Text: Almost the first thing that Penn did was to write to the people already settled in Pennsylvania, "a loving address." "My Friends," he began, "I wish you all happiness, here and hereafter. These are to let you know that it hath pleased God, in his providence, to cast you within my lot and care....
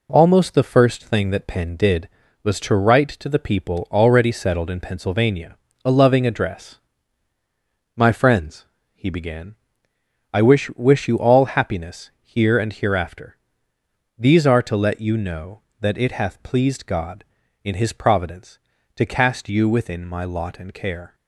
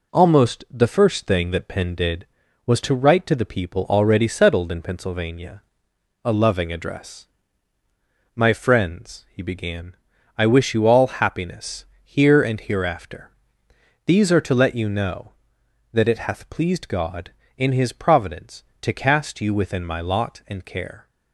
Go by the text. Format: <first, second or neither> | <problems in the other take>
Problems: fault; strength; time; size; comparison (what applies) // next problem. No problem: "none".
second | says "wish" twice; at 10.7 s